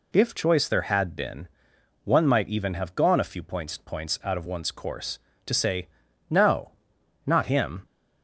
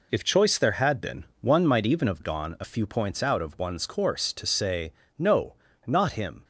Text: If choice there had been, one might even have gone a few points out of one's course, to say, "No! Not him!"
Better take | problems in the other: second | says "points" twice; at 3.7 s

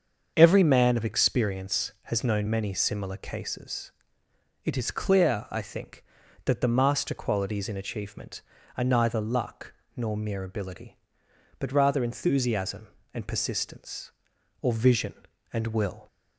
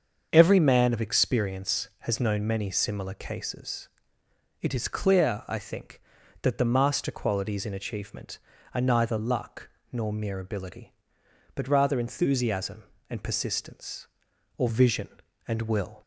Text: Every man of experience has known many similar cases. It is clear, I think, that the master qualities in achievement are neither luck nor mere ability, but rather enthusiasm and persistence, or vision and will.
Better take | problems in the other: neither | starts louder than the rest; the same in both // pauses between "luck" and "nor"; slight; the same in both

